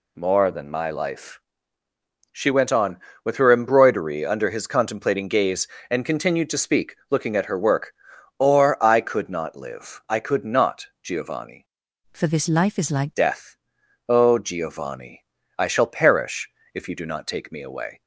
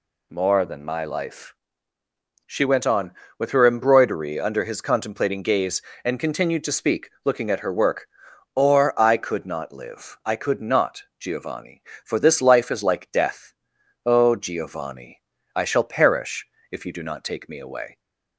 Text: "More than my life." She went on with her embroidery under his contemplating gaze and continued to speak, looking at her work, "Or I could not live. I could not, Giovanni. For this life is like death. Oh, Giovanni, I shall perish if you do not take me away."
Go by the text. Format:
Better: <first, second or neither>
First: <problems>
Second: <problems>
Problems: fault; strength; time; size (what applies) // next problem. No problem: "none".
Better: second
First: changes voice from "For" to "like"; from 12.1 to 13.1 s; 1.0 s long // pauses between "perish" and "if"; slight; at 16.4 s; 0.24 s long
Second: pauses between "perish" and "if"; slight; at 16.4 s; 0.24 s long